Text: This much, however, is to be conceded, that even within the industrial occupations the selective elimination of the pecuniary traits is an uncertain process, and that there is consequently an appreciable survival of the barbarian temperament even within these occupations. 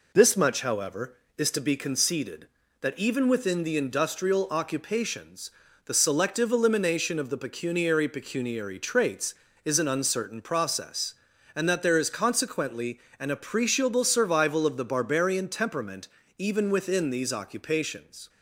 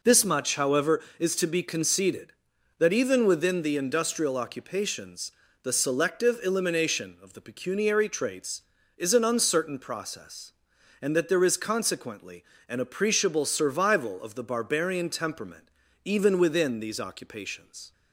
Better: second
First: pauses between "occupations" and "the"; slight; at 5.5 s; 0.34 s long // says "pecuniary" twice; at 8.0 s // pauses between "consequently" and "an"; slight; at 12.9 s; 0.20 s long // pauses between "temperament" and "even"; slight; at 16.0 s; 0.30 s long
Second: pauses between "occupations" and "the"; slight; at 5.3 s; 0.30 s long // pauses between "consequently" and "an"; slight; at 12.4 s; 0.22 s long // pauses between "temperament" and "even"; slight; at 15.6 s; 0.36 s long

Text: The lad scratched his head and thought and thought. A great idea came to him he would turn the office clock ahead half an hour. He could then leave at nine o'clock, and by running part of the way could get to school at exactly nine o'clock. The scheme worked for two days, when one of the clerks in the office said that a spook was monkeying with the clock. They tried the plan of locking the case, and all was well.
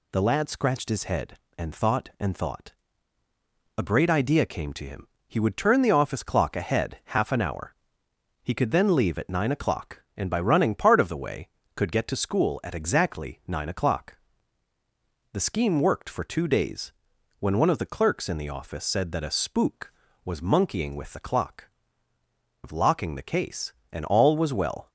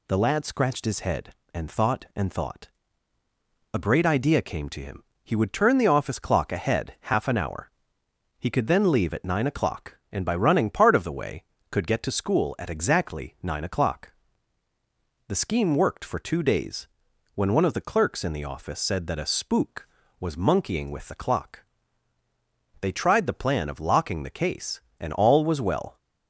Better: second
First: pauses between "him" and "he"; slight; at 5.0 s; 0.22 s long // skips "They tried the plan"; at 22.1 s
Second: pauses between "him" and "he"; slight; at 5.0 s; 0.22 s long

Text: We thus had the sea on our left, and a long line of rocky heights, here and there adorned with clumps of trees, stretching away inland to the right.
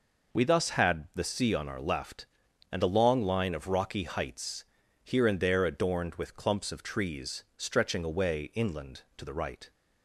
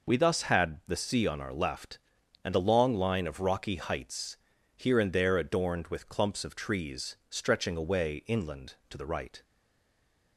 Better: first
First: none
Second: stays silent after the last word; slight; from 9.4 s on; 0.9 s long

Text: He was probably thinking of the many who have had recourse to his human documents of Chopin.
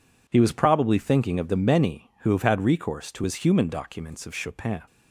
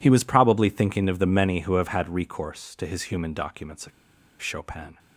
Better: first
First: none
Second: pauses between "of" and "Chopin"; noticeable; at 3.9 s; 0.51 s long

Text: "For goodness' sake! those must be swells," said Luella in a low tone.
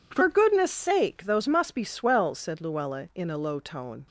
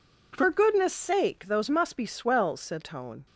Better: first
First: none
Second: skips "Luella in a low"; at 2.8 s

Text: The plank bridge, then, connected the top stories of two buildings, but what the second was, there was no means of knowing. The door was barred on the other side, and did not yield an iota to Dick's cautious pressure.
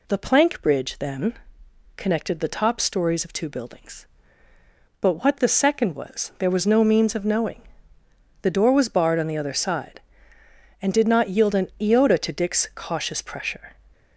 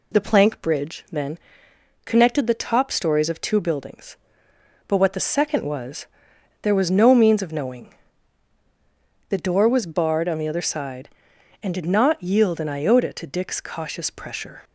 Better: neither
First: none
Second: none

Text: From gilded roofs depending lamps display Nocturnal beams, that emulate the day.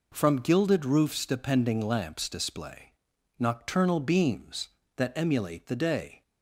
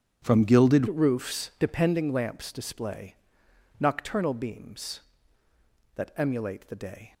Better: first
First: pauses between "display" and "Nocturnal"; noticeable; at 2.9 s; 0.46 s long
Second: starts louder than the rest; strong; until 1.2 s; 9 dB // changes voice at "roofs"; from 0.8 s on; 6.3 s long // pauses between "display" and "Nocturnal"; noticeable; at 3.1 s; 0.66 s long

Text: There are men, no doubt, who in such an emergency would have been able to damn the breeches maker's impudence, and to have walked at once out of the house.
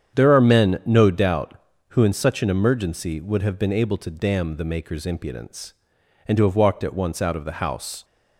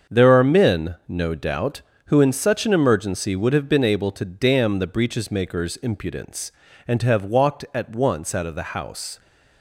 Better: second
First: starts louder than the rest; strong; until 1.2 s; 8.5 dB // skips "breeches"; at 4.6 s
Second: starts louder than the rest; until 1.2 s; 7 dB

